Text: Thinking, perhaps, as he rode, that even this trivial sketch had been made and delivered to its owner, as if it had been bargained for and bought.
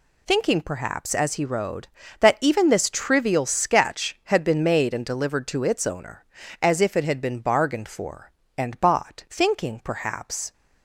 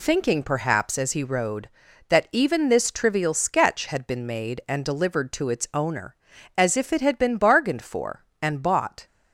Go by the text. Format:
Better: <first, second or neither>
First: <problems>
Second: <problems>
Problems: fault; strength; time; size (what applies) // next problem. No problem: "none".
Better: second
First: goes on to say "Thinking perhaps"; noticeable; from 9.3 s on; 1.2 s long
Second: none